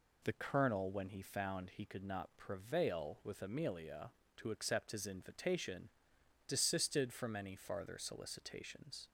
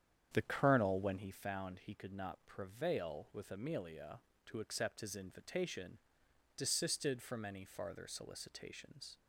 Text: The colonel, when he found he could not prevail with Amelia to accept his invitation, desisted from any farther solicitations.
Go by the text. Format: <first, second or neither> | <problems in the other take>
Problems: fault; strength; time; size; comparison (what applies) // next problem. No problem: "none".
first | starts louder than the rest; strong; until 1.4 s; 9 dB